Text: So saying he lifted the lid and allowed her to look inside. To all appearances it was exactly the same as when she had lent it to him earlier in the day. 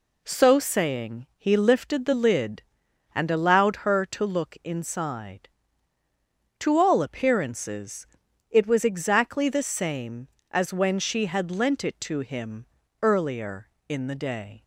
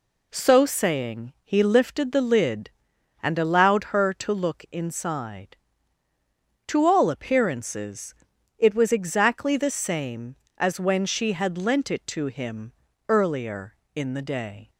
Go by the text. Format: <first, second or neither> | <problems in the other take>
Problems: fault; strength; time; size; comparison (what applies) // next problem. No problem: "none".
neither | pauses between "appearances" and "it"; the same in both // pauses between "him" and "earlier"; slight; the same in both